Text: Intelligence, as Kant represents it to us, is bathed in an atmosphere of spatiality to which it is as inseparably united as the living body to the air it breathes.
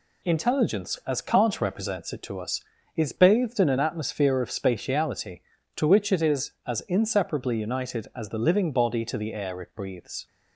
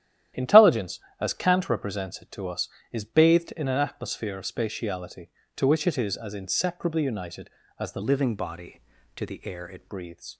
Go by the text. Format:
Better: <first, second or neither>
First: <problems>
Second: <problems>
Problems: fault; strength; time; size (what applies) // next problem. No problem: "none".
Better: first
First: none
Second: starts louder than the rest; strong; until 1.5 s; 11.5 dB // changes voice from "living" to "it"; from 8.0 to 9.8 s; 1.8 s long